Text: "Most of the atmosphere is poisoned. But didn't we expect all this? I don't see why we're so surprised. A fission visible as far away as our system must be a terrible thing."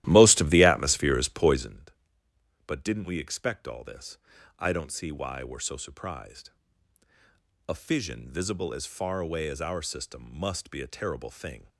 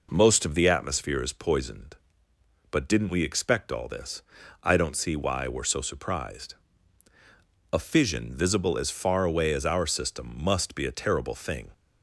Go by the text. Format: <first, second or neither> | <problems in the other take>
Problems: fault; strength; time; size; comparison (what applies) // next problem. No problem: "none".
second | starts louder than the rest; strong; until 1.9 s; 14.5 dB